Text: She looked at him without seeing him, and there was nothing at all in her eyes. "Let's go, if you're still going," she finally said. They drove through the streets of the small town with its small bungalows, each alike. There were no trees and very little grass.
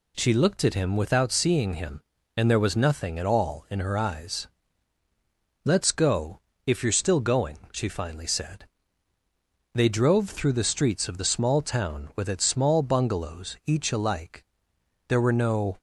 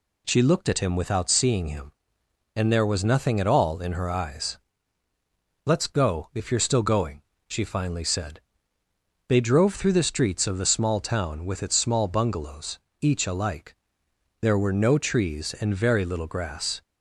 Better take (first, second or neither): second